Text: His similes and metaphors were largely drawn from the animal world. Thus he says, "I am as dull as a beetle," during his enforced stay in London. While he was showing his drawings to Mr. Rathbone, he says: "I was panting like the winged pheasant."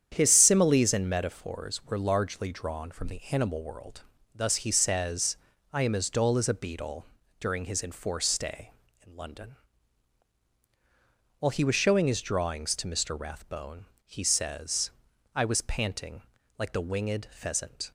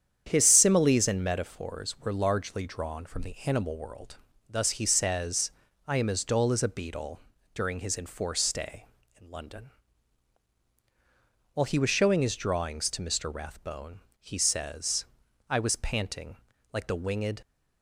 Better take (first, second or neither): first